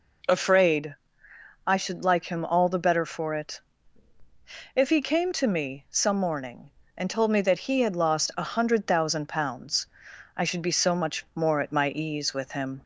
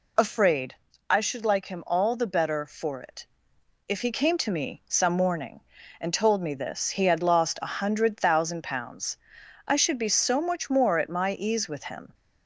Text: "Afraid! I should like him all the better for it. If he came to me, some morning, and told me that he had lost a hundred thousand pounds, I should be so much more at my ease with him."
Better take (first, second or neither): first